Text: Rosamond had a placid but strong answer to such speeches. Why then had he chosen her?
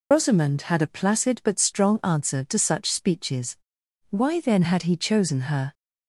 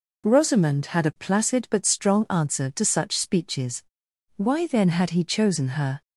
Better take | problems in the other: second | loses the start of "Rosamond"; at 0.1 s; 115 ms

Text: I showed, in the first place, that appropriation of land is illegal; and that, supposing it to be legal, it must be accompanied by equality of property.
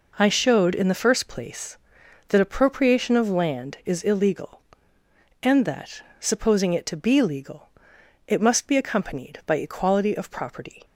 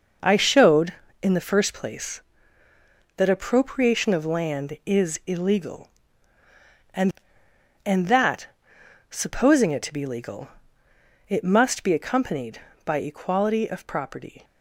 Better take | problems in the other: first | says "and" twice; at 7.8 s

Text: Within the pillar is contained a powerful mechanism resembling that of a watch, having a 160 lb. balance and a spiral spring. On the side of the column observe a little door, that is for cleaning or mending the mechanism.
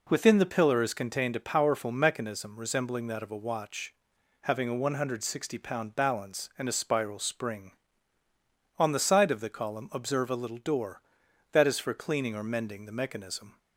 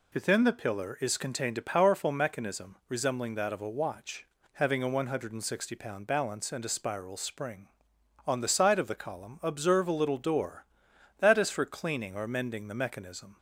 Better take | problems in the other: neither | none

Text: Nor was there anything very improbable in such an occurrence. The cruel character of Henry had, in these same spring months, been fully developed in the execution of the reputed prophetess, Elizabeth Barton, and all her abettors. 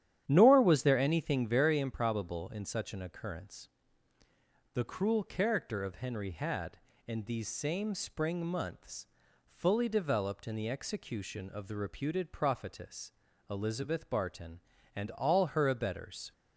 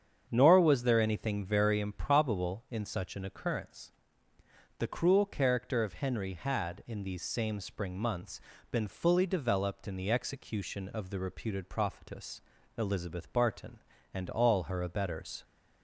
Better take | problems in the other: second | starts louder than the rest; strong; until 1.2 s; 10.5 dB; strong in the second // skips "been"; at 9.2 s

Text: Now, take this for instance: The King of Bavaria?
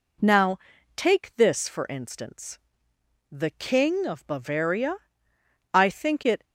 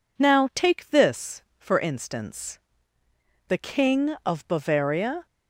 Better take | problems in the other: second | goes on to say "I think it"; noticeable; from 5.7 s on; 0.70 s long

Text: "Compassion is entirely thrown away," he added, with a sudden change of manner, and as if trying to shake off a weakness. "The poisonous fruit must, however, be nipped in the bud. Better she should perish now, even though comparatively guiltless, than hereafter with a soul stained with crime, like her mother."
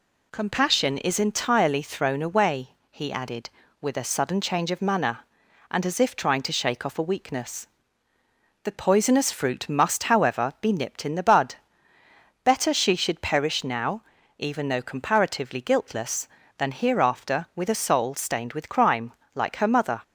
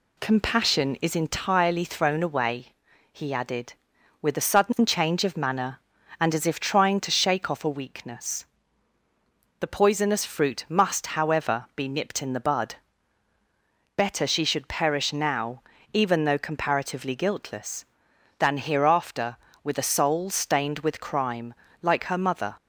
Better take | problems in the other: neither | none

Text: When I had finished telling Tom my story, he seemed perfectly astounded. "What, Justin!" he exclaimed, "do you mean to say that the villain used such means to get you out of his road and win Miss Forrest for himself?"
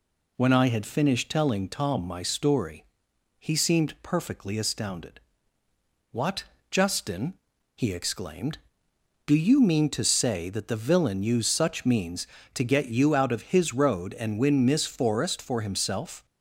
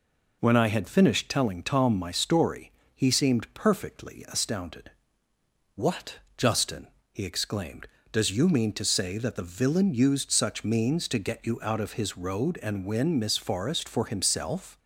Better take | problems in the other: first | says "does" for "do"; at 8.1 s

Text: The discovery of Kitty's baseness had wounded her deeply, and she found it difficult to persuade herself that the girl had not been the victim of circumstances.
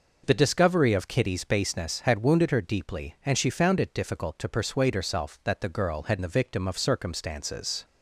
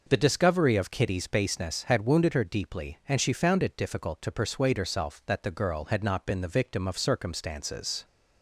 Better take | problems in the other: second | skips "not been"; at 6.1 s

